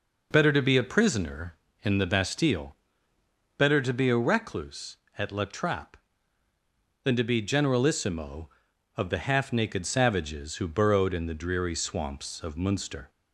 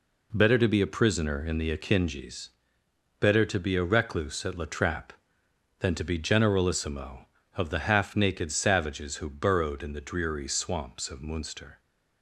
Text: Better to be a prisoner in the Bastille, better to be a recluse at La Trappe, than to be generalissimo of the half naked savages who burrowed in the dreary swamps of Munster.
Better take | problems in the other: first | says "Akinjis" for "Bastille"; at 1.7 s

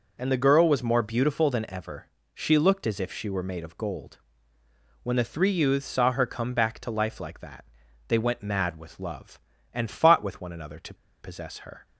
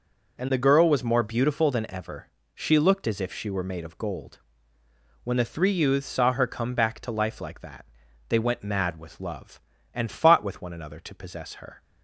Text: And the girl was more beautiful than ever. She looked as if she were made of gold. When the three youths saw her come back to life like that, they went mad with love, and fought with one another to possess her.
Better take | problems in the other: second | pauses between "to" and "possess"; slight; at 10.9 s; 0.27 s long

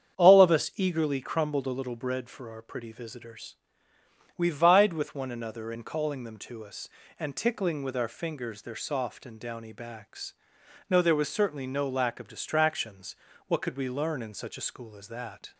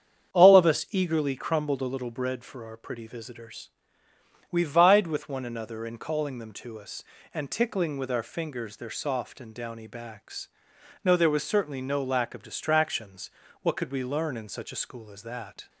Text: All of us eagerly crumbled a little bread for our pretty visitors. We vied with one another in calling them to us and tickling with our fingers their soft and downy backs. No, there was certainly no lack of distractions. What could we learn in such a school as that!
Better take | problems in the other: neither | starts louder than the rest; strong; the same in both

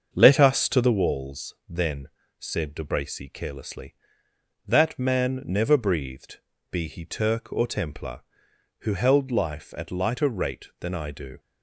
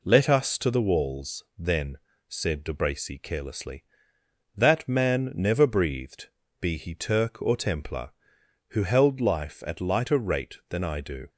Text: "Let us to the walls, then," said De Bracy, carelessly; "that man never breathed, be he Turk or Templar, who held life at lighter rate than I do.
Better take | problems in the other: second | starts louder than the rest; until 1.0 s; 6.5 dB

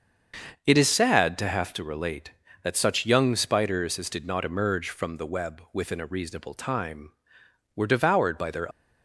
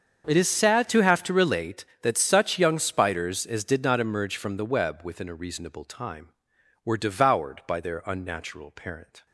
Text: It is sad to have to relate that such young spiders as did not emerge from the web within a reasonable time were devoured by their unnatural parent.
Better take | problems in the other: second | starts louder than the rest; until 1.6 s; 6.5 dB; also in the second // stops before "unnatural parent"; at 8.7 s

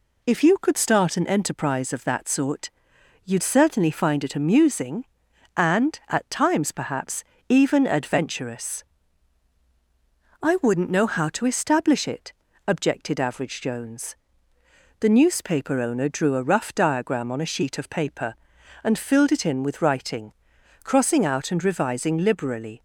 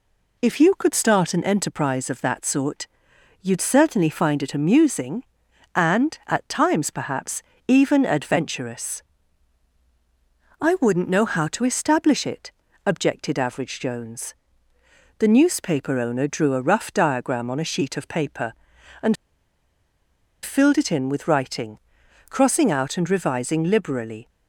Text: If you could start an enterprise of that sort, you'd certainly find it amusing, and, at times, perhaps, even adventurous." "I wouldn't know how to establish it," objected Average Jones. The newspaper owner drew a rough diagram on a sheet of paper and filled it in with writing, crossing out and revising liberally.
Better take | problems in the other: first | pauses between "and" and "filled"; strong; at 19.1 s; 1.2 s long

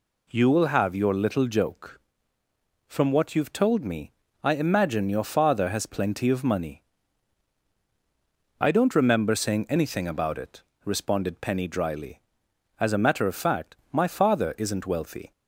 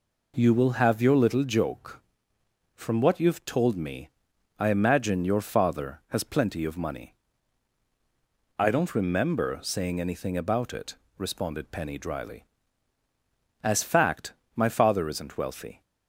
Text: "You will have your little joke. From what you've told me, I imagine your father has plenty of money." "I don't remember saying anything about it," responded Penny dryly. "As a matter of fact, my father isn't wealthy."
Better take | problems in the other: first | skips "a matter of"; at 13.8 s

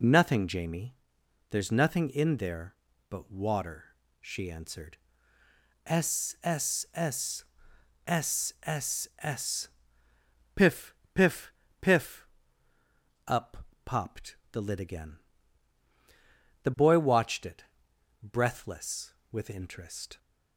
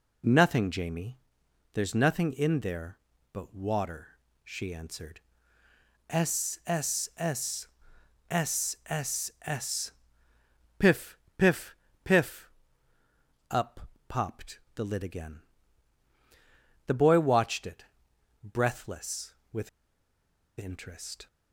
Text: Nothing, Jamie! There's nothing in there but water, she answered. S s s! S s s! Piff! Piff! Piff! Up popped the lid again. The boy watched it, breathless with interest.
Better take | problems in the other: first | pauses between "Up" and "popped"; slight; at 13.8 s; 0.28 s long; slight in the first // pauses between "popped" and "the"; slight; at 14.6 s; 0.16 s long; slight in the first // pauses between "with" and "interest"; noticeable; at 19.6 s; 0.89 s long

